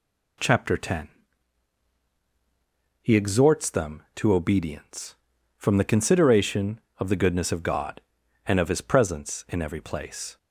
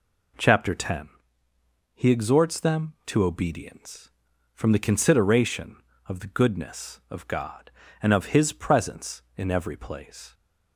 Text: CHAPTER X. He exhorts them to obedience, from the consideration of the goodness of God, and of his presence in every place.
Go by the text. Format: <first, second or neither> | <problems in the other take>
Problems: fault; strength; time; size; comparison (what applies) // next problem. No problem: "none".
neither | none